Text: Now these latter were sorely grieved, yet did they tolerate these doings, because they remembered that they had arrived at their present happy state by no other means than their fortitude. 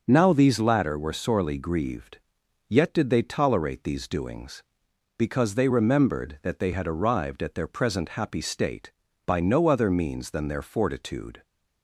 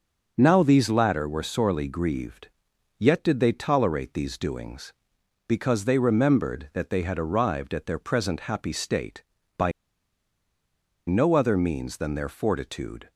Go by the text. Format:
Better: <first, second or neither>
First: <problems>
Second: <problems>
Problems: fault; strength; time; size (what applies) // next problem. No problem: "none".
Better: first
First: starts louder than the rest; until 1.0 s; 6.5 dB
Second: starts louder than the rest; until 1.3 s; 6.5 dB // pauses between "by" and "no"; strong; at 9.7 s; 1.3 s long